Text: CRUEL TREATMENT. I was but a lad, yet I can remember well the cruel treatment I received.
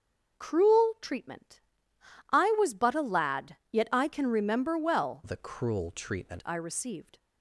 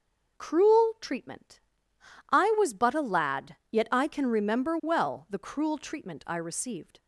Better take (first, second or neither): second